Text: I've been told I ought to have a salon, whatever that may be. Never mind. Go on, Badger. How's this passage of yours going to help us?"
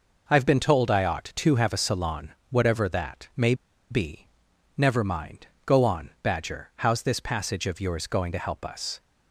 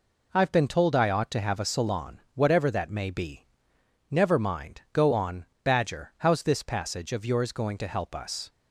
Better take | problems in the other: second | pauses between "may" and "be"; at 3.5 s; 0.36 s long

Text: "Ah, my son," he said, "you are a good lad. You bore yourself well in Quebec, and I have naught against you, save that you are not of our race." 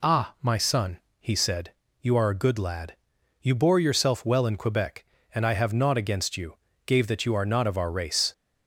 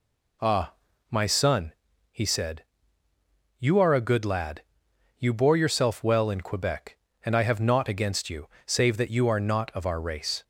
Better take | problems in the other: second | says "gave" for "save"; at 6.8 s

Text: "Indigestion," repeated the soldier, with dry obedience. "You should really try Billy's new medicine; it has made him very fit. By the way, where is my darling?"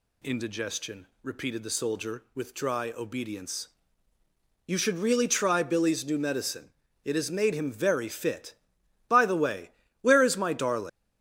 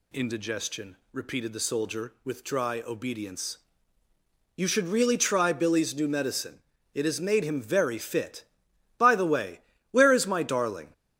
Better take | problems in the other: second | leaves "darling" unfinished; at 10.8 s; 130 ms

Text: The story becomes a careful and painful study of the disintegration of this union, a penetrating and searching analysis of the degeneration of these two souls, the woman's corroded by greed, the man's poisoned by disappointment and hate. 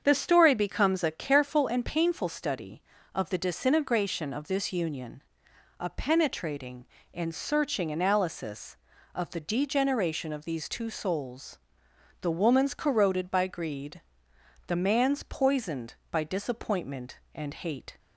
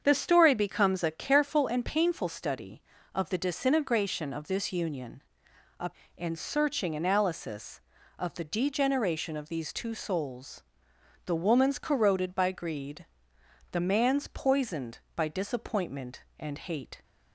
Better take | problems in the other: first | starts louder than the rest; strong; until 1.0 s; 7 dB; strong in the first // skips "penetrating"; at 6.0 s

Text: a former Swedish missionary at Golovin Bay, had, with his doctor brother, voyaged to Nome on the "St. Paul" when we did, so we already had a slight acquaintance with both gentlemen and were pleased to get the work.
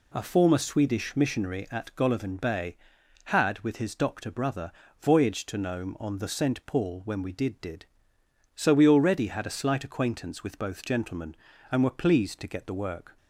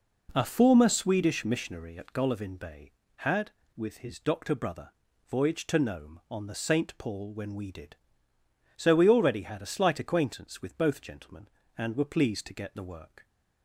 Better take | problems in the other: second | says "did" twice; at 7.6 s

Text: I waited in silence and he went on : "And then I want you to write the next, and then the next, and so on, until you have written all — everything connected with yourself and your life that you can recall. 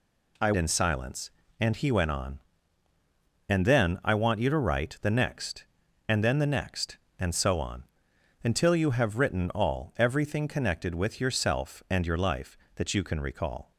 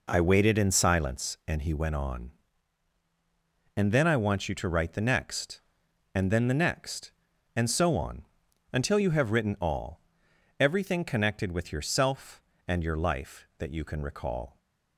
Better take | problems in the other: second | skips "waited"; at 0.5 s

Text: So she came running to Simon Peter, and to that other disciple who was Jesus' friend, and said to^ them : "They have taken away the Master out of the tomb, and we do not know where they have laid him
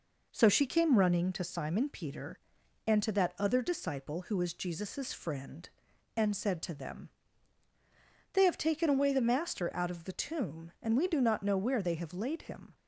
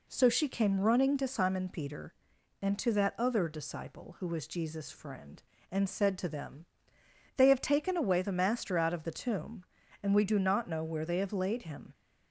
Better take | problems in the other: neither | none

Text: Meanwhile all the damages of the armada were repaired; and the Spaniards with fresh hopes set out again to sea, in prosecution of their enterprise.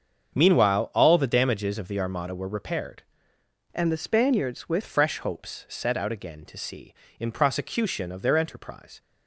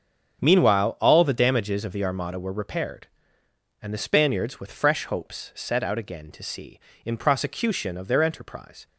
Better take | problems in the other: second | starts louder than the rest; strong; until 1.3 s; 7 dB; strong in the second // changes voice from "and" to "with"; from 3.7 to 4.8 s; 1.1 s long

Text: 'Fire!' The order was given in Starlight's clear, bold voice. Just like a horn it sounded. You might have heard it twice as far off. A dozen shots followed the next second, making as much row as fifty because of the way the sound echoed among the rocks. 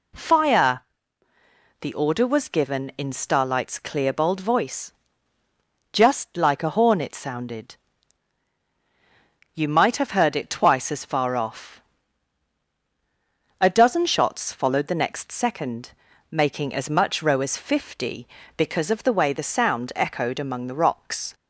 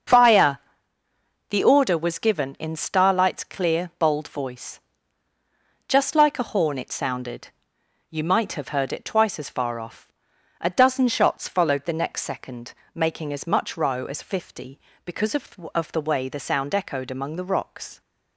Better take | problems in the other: first | starts louder than the rest; until 1.9 s; 7 dB // says "of" twice; at 15.7 s

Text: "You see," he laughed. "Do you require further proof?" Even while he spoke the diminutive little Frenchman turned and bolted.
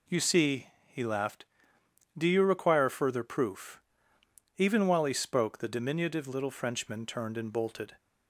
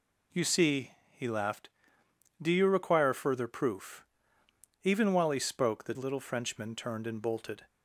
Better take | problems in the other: first | skips "diminutive"; at 5.9 s

